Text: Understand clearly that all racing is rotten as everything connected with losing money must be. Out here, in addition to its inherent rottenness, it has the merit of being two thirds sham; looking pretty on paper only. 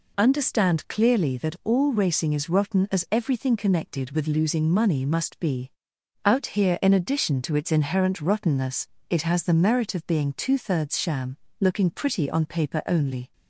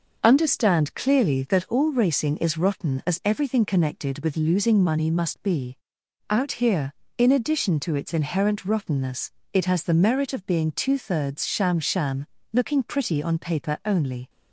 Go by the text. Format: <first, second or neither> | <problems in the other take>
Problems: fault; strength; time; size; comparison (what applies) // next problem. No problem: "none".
first | says "sham" twice; at 11.7 s